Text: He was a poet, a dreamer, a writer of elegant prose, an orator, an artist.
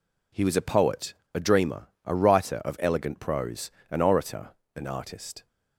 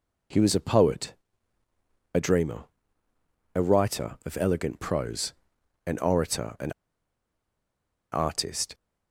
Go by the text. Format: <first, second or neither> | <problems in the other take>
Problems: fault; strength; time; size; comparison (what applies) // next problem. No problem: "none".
first | pauses between "an" and "artist"; strong; at 6.7 s; 1.4 s long